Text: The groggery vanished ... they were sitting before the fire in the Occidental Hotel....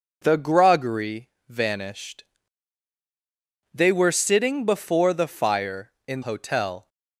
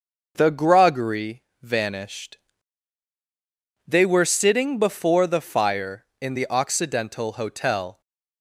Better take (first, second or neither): second